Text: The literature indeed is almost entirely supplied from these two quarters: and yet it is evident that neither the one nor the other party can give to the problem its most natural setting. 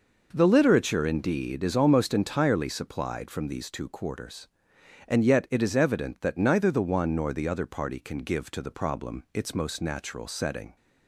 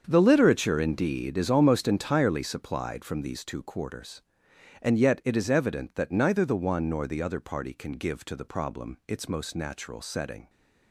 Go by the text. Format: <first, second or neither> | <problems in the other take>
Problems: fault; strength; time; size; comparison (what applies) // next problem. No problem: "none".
first | gets quieter; strong; throughout; 12 dB